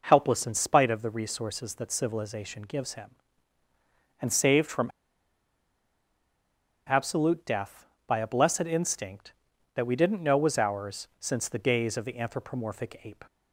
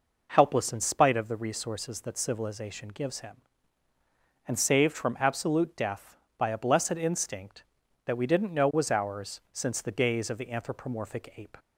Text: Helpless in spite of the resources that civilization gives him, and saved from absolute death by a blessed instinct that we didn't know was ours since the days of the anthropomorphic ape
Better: second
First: pauses between "from" and "absolute"; strong; at 4.9 s; 1.9 s long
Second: none

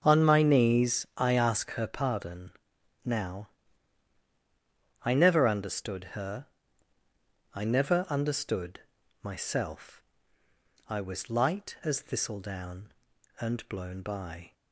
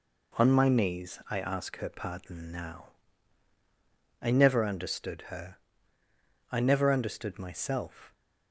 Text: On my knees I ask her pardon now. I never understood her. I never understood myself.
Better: second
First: starts louder than the rest; until 1.0 s; 7 dB // pauses between "pardon" and "now"; noticeable; at 2.5 s; 0.54 s long // pauses between "understood" and "myself"; at 8.8 s; 0.42 s long // goes on to say "I was light as thistledown and blown by"; strong; from 10.8 s on; 3.6 s long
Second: none

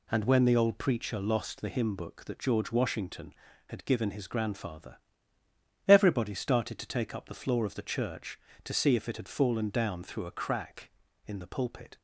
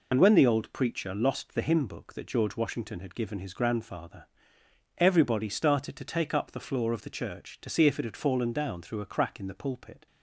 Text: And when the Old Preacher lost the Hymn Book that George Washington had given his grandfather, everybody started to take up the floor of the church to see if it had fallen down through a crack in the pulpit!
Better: first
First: none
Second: loses the start of "And"; at 0.1 s; 35 ms

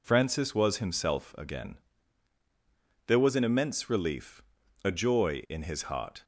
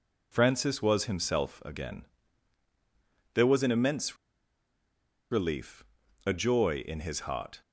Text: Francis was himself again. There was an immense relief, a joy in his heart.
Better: first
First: none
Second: pauses between "immense" and "relief"; at 4.1 s; 1.1 s long

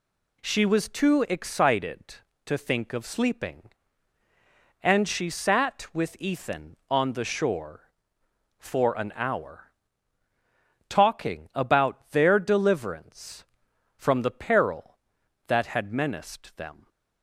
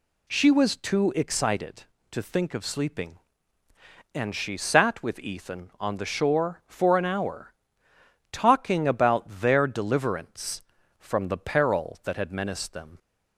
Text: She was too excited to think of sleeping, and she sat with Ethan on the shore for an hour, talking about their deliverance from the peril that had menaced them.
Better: neither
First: none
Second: none

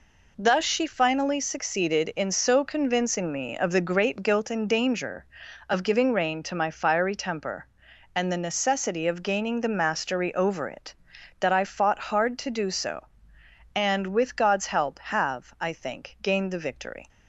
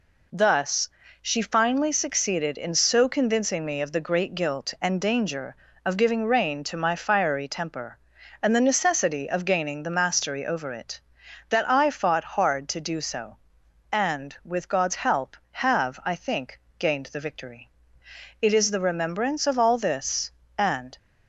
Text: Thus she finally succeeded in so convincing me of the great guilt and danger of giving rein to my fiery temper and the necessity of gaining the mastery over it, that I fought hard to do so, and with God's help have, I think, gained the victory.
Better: first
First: none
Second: pauses between "Thus" and "she"; slight; at 0.8 s; 0.32 s long // goes on to say "It is the remembrance of all this and"; strong; from 18.4 s on; 2.5 s long

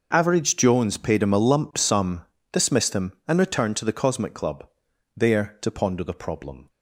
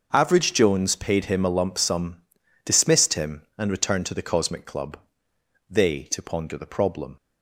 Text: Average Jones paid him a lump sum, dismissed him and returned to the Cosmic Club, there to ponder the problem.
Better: first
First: starts louder than the rest; noticeable; until 1.1 s; 6 dB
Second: starts louder than the rest; noticeable; until 1.1 s; 6 dB // says "they" for "there"; at 5.7 s

